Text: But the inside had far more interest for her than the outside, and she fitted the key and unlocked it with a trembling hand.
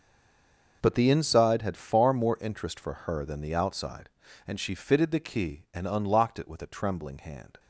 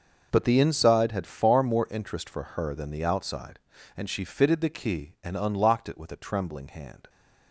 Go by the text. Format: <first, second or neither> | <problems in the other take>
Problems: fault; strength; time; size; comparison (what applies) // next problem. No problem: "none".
second | stays silent before the first word; slight; until 0.8 s; 0.8 s long